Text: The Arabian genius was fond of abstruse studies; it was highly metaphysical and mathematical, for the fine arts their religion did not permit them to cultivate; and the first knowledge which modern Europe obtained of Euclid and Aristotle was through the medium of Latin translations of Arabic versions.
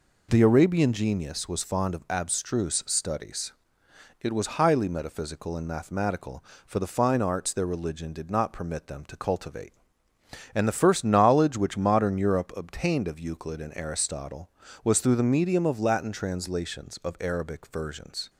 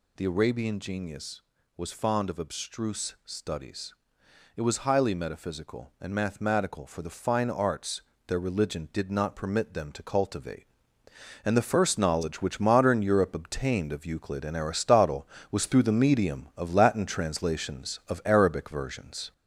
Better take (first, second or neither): first